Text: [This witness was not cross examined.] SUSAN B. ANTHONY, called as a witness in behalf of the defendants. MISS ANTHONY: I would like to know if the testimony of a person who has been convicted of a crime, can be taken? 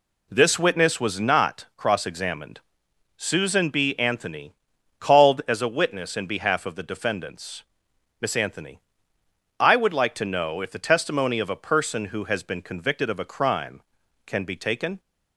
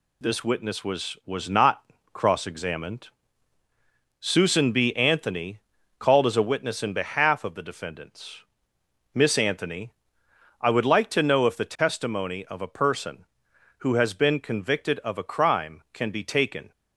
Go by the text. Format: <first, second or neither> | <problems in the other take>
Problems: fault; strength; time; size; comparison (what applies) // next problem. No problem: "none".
first | says "was" twice; at 1.2 s // pauses between "not" and "cross"; slight; at 1.8 s; 0.30 s long